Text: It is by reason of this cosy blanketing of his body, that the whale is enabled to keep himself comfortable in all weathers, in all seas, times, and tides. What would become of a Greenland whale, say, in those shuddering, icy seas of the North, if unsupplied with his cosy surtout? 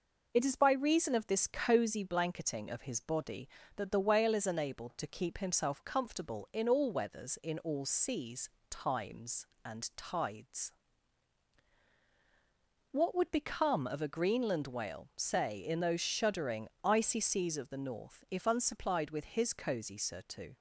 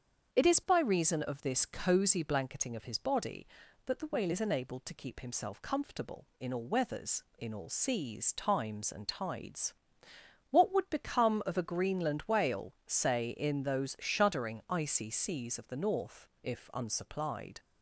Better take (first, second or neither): first